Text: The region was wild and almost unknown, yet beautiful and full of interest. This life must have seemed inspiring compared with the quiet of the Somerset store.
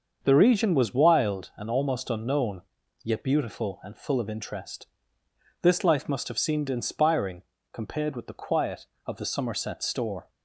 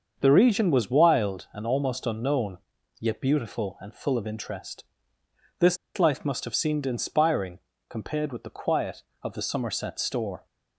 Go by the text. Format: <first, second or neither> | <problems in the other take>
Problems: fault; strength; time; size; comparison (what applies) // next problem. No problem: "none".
first | starts louder than the rest; until 1.2 s; 6.5 dB; also in the first // pauses between "This" and "life"; slight; at 5.7 s; 0.20 s long // pauses between "inspiring" and "compared"; slight; at 7.5 s; 0.30 s long; slight in the first